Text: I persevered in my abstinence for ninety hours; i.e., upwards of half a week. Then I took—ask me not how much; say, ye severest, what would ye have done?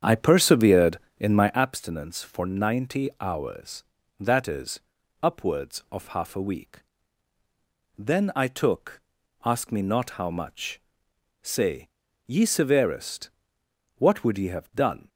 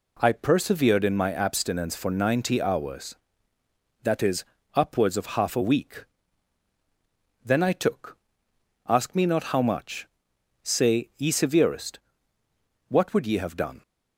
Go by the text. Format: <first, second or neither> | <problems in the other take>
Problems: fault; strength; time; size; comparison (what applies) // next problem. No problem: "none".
second | starts louder than the rest; strong; until 1.6 s; 8 dB